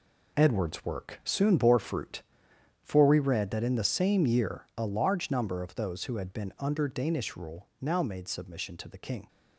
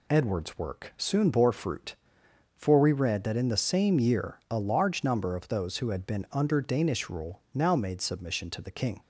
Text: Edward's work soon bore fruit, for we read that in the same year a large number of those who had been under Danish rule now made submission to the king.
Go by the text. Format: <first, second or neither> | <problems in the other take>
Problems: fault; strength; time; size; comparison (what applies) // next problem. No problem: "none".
second | gets quieter; strong; throughout; 9.5 dB